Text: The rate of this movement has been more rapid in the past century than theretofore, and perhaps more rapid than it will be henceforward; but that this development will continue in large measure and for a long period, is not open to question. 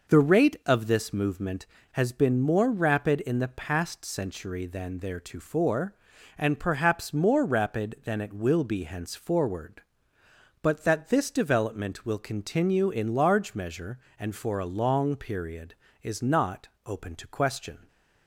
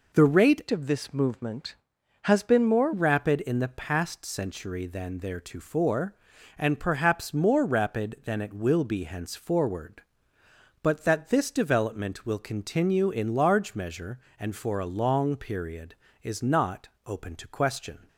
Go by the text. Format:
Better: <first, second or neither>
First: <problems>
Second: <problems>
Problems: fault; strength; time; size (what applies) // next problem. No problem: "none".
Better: first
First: pauses between "not" and "open"; slight; at 16.6 s; 0.16 s long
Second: changes voice from "of" to "more"; from 0.7 to 2.9 s; 2.2 s long // pauses between "not" and "open"; slight; at 16.8 s; 0.16 s long